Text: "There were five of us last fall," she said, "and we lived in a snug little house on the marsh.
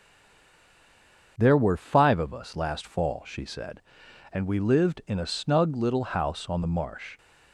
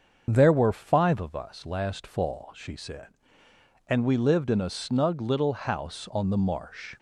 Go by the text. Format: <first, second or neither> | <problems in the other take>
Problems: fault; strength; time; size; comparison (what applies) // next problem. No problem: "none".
second | stays silent before the first word; noticeable; until 1.3 s; 1.3 s long // starts louder than the rest; until 2.3 s; 7 dB; also in the second